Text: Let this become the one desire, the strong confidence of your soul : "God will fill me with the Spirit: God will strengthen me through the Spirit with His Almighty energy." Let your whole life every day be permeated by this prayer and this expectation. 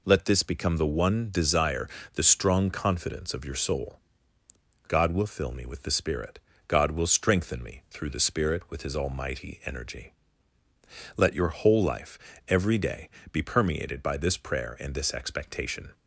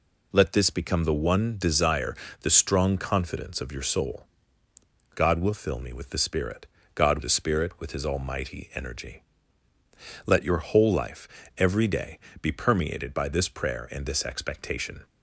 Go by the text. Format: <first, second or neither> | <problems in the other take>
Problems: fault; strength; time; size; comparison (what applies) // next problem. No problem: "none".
first | skips "will strengthen me through"; at 7.1 s // pauses between "life" and "every"; slight; at 11.2 s; 0.30 s long; slight in the first // pauses between "day" and "be"; slight; at 12.1 s; 0.24 s long; slight in the first